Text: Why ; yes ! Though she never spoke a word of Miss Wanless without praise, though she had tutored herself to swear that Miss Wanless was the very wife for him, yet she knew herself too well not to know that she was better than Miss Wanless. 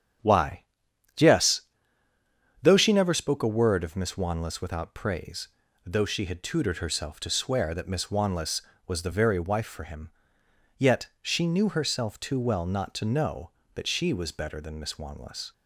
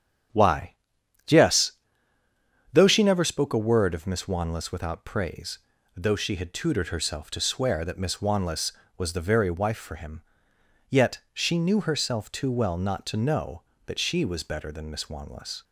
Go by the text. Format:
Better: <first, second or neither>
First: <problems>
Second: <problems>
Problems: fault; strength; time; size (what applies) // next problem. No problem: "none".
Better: neither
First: starts louder than the rest; strong; until 2.7 s; 9 dB // pauses between "yet" and "she"; slight; at 11.0 s; 0.16 s long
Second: starts louder than the rest; strong; until 2.8 s; 9 dB // pauses between "yet" and "she"; slight; at 11.1 s; 0.16 s long